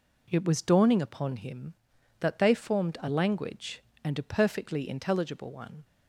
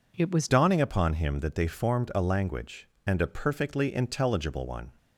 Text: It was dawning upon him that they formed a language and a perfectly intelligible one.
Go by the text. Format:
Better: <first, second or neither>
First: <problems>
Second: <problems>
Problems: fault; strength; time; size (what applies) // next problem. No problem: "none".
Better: first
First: none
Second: changes voice at "dawning"; from 0.4 s on; 4.5 s long